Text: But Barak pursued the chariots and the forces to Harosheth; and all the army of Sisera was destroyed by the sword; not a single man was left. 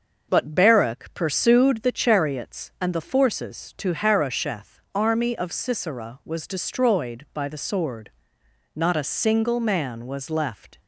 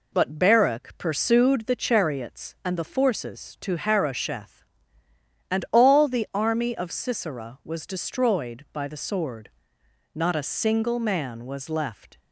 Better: second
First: starts louder than the rest; until 1.3 s; 6.5 dB // skips "and all the"; at 4.8 s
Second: none

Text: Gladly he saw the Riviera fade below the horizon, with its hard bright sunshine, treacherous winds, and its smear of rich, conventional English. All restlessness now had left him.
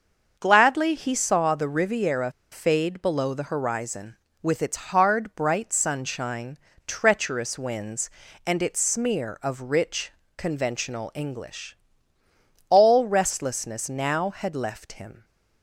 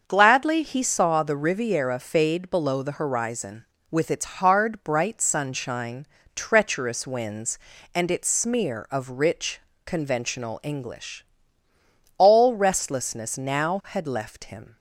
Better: second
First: starts louder than the rest; until 1.3 s; 6.5 dB // pauses between "Riviera" and "fade"; slight; at 2.3 s; 0.20 s long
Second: starts louder than the rest; until 1.0 s; 6.5 dB

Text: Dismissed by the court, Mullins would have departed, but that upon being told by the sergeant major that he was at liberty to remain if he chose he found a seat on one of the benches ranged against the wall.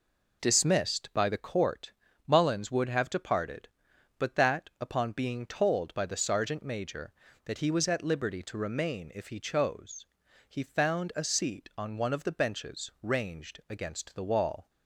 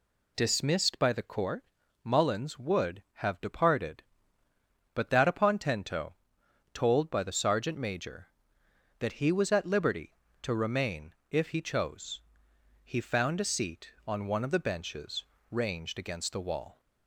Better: first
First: pauses between "chose" and "he"; at 10.0 s; 0.42 s long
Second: says "tento" for "being"; at 5.5 s // pauses between "remain" and "if"; slight; at 11.1 s; 0.16 s long // pauses between "chose" and "he"; noticeable; at 12.1 s; 0.64 s long // pauses between "benches" and "ranged"; slight; at 15.2 s; 0.26 s long

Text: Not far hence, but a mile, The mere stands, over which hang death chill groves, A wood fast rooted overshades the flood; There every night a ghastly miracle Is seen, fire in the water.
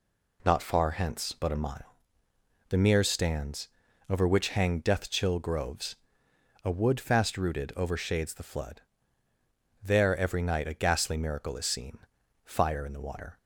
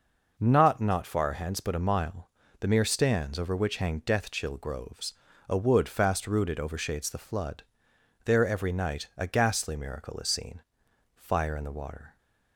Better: first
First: none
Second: says "Not" twice; at 0.7 s

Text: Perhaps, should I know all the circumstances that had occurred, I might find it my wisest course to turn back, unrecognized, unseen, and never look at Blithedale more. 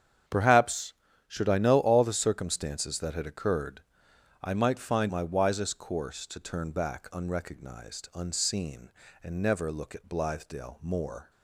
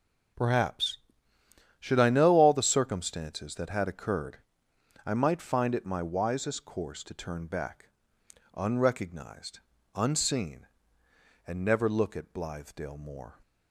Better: second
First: starts louder than the rest; strong; until 1.6 s; 8 dB // skips "it"; at 5.0 s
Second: none

